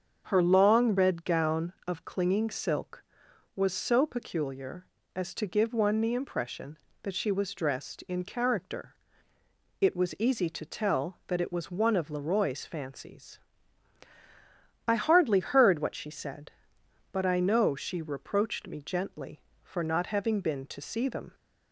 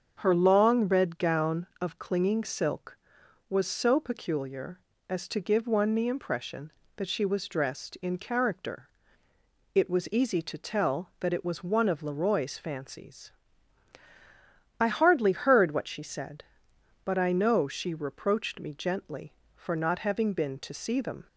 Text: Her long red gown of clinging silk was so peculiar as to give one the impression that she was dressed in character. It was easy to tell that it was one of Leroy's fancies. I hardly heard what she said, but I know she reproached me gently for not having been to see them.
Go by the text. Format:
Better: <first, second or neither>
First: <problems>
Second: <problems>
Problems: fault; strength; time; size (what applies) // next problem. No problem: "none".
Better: neither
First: starts louder than the rest; until 1.3 s; 7 dB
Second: starts louder than the rest; until 1.2 s; 6.5 dB